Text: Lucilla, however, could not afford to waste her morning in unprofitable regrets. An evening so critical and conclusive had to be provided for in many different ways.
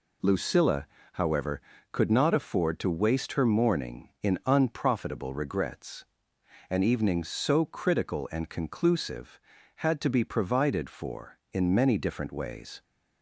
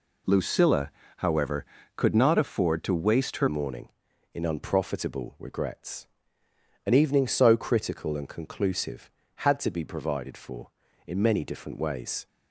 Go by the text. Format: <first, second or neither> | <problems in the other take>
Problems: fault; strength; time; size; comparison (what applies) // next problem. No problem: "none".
first | changes voice at "morning"; from 3.4 s on; 8.8 s long